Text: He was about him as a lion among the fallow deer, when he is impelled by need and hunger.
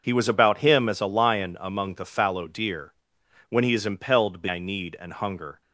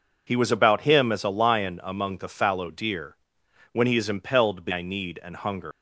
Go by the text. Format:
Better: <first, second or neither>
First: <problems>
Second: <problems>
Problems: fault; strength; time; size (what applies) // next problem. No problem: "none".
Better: first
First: none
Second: leaves "hunger" unfinished; at 5.7 s; 125 ms